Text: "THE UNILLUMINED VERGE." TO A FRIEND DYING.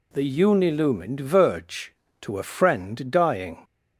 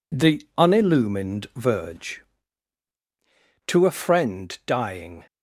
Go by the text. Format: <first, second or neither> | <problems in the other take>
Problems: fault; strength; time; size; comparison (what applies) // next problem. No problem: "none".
neither | none